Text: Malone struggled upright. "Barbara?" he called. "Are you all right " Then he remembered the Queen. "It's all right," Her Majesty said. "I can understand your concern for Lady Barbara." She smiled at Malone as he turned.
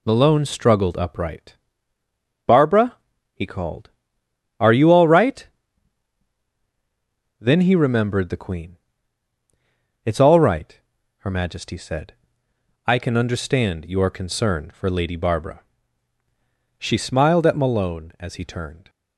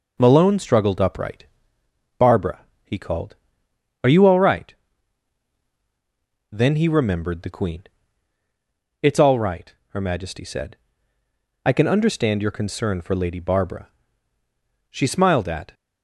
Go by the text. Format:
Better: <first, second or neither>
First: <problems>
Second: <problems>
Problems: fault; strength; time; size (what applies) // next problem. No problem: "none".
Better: first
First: none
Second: stops before "Malone as he turned"; at 15.7 s